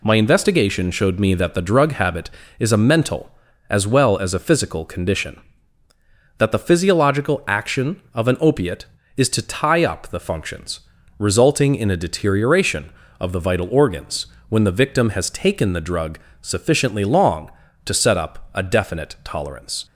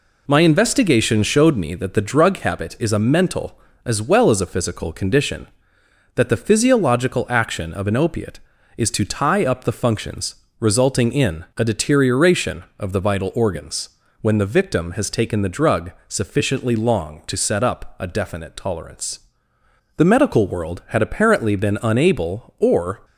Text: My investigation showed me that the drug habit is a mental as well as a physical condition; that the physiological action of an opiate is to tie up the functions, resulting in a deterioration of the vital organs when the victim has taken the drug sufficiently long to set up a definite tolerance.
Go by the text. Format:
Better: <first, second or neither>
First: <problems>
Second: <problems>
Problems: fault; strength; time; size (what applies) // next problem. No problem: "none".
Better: first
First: pauses between "organs" and "when"; slight; at 14.2 s; 0.24 s long // pauses between "drug" and "sufficiently"; slight; at 16.1 s; 0.22 s long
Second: pauses between "organs" and "when"; slight; at 13.9 s; 0.30 s long // pauses between "drug" and "sufficiently"; slight; at 15.9 s; 0.16 s long // goes on to say "The medical world had apparently been unable or"; strong; from 19.9 s on; 3.0 s long